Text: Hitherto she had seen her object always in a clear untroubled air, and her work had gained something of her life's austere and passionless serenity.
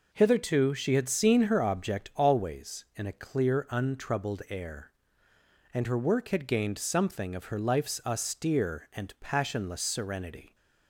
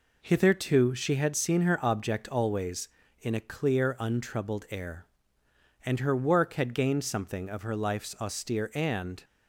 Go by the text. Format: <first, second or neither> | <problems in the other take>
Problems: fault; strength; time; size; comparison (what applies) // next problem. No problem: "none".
first | stops before "passionless serenity"; at 9.2 s